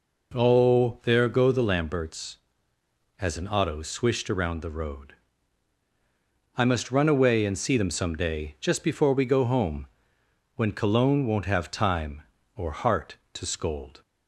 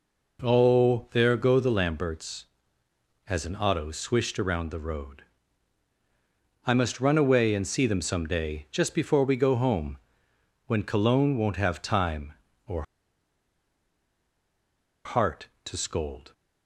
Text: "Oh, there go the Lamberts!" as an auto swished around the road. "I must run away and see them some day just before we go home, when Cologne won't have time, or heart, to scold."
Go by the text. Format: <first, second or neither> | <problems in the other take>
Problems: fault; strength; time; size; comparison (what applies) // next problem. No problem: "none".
first | pauses between "or" and "heart"; strong; at 12.8 s; 2.2 s long